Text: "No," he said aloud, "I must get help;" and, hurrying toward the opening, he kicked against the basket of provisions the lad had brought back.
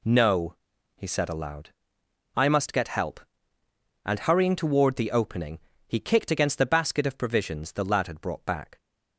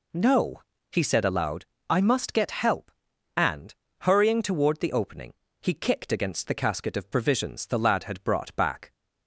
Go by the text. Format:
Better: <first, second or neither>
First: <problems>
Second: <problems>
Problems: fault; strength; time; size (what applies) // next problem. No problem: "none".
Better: first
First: none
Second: says "casket" for "basket"; at 6.5 s